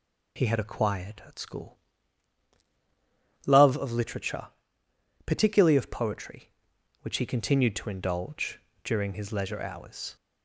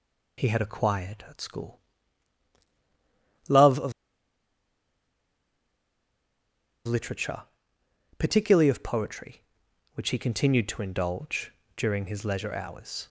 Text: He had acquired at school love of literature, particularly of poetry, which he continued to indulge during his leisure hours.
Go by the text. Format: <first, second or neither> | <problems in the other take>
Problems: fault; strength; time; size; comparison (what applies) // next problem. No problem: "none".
first | pauses between "school" and "love"; strong; at 1.8 s; 1.6 s long; strong in the first // pauses between "of" and "literature"; strong; at 3.9 s; 2.9 s long // pauses between "indulge" and "during"; slight; at 11.4 s; 0.28 s long; slight in the first